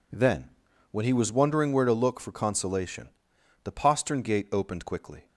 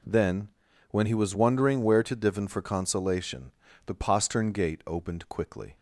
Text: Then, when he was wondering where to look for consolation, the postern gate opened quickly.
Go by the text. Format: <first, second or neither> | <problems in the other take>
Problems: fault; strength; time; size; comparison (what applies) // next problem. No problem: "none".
first | says "divin" for "look"; at 2.1 s